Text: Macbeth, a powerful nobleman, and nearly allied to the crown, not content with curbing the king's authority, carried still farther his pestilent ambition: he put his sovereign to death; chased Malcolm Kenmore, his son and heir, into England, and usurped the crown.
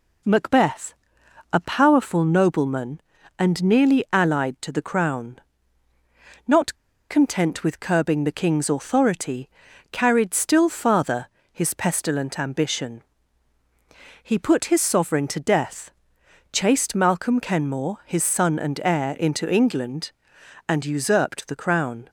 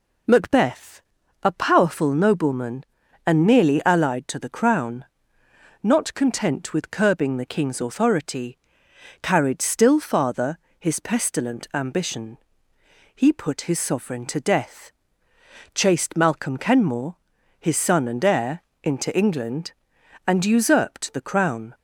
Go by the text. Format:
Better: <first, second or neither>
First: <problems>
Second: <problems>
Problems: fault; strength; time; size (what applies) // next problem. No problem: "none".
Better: second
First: pauses between "not" and "content"; at 6.7 s; 0.36 s long // pauses between "farther" and "his"; slight; at 11.2 s; 0.24 s long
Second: pauses between "farther" and "his"; slight; at 10.5 s; 0.22 s long